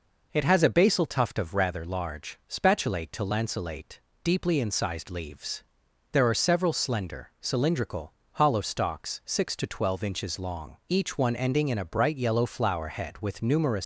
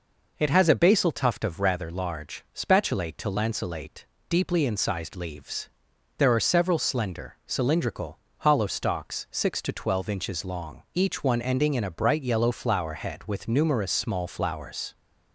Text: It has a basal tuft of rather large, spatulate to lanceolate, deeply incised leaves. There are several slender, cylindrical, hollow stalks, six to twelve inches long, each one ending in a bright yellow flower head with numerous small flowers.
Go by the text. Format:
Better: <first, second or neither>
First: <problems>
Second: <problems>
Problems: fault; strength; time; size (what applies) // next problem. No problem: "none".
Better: second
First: stops before "small flowers"; at 13.8 s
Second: none